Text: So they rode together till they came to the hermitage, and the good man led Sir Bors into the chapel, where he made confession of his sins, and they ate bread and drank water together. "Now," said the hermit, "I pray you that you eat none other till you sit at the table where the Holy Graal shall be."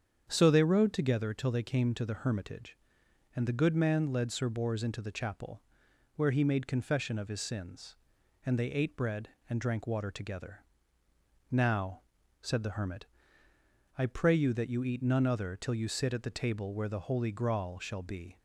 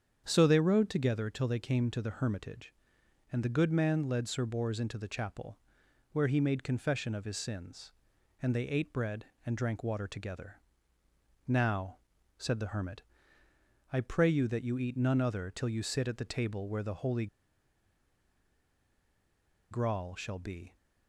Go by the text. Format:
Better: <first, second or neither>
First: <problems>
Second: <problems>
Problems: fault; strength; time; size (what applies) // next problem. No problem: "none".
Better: first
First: starts louder than the rest; strong; until 1.2 s; 7.5 dB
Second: starts louder than the rest; strong; until 1.2 s; 7.5 dB // pauses between "Holy" and "Graal"; strong; at 17.2 s; 2.4 s long